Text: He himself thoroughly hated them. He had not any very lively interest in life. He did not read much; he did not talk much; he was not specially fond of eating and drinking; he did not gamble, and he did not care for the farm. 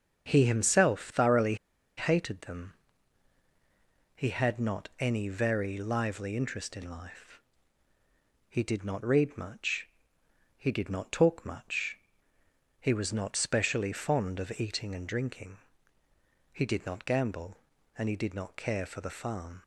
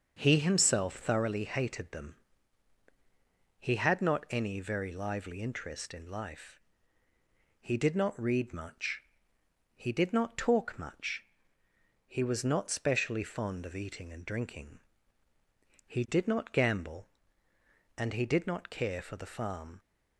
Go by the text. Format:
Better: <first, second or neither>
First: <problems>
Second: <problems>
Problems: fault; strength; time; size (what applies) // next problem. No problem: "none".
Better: second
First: starts louder than the rest; strong; until 1.3 s; 7 dB // pauses between "thoroughly" and "hated"; at 1.5 s; 0.42 s long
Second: starts louder than the rest; until 1.2 s; 6.5 dB